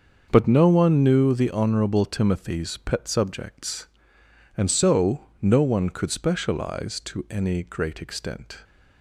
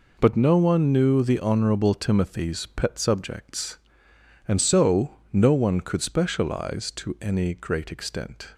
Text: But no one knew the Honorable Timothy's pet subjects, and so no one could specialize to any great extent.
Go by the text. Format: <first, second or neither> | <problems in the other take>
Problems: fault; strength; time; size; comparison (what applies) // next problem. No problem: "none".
second | starts louder than the rest; until 1.4 s; 6.5 dB // pauses between "so" and "no"; slight; at 5.2 s; 0.15 s long; slight in the second